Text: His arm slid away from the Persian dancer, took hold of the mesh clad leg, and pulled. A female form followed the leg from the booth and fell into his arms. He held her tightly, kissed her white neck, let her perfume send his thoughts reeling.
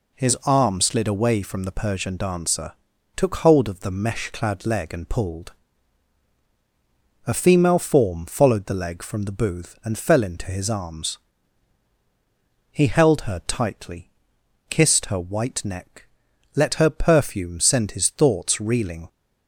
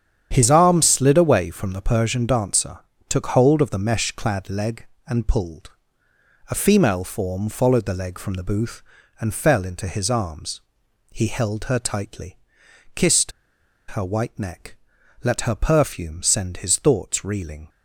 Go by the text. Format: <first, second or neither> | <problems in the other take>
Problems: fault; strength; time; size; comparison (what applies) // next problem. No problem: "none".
first | starts louder than the rest; strong; until 1.3 s; 9 dB // pauses between "kissed" and "her"; noticeable; at 13.3 s; 0.57 s long